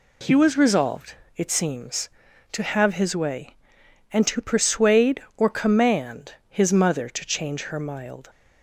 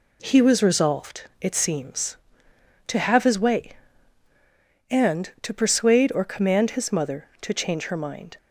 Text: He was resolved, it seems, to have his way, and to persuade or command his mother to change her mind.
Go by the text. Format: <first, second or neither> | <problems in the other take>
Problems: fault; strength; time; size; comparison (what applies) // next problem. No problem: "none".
second | says "mild" for "mind"; at 7.7 s